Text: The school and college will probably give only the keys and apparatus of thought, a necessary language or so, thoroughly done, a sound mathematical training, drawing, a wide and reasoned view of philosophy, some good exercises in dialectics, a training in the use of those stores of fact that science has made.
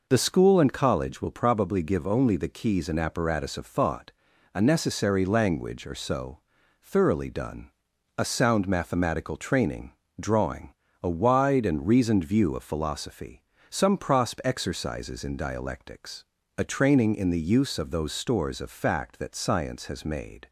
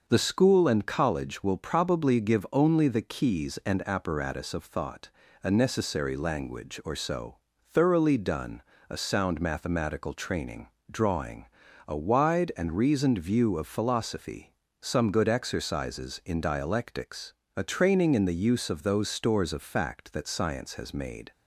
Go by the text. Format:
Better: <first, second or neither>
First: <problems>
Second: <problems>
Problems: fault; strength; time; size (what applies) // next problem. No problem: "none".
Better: second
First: says "prosp" for "good"; at 13.9 s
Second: none